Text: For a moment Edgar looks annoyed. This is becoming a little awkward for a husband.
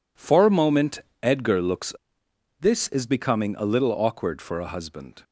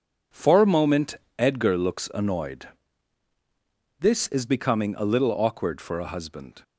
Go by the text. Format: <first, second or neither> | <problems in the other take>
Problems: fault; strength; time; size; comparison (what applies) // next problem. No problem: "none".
second | pauses between "moment" and "Edgar"; slight; at 0.9 s; 0.24 s long; slight in the second // skips "annoyed"; at 2.2 s